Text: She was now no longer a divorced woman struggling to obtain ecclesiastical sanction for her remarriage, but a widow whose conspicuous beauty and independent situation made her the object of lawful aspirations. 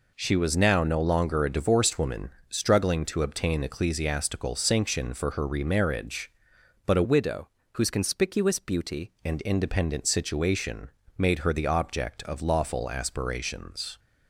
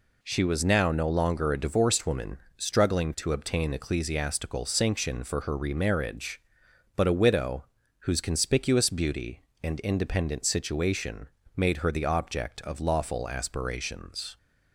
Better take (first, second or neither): second